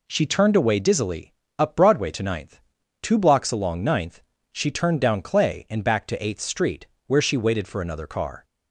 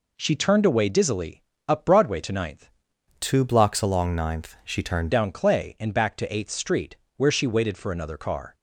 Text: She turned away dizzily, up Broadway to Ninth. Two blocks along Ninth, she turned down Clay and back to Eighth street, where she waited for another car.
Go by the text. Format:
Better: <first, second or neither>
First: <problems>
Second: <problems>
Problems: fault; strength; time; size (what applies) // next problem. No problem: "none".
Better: first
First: none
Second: changes voice from "Two" to "turned"; from 3.2 to 5.1 s; 1.9 s long